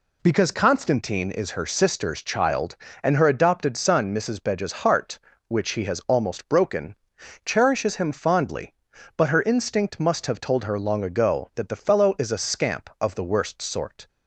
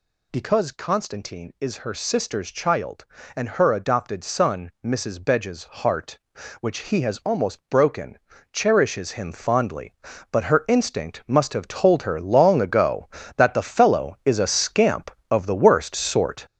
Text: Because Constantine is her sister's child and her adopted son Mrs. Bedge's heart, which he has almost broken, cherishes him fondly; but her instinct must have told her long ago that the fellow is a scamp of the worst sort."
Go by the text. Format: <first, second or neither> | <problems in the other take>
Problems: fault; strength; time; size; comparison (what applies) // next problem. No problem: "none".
first | gets louder; noticeable; throughout; 6 dB